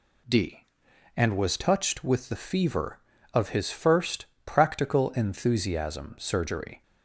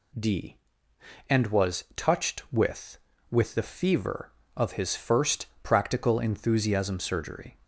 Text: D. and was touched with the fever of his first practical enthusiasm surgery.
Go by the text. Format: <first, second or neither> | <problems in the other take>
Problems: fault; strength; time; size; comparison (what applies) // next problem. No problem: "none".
first | says "with" twice; at 3.2 s // pauses between "first" and "practical"; slight; at 5.4 s; 0.16 s long; slight in the first